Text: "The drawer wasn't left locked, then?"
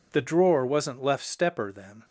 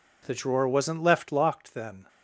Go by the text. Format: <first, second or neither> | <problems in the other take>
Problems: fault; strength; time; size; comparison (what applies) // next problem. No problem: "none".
second | says "stepper" for "locked"; at 1.2 s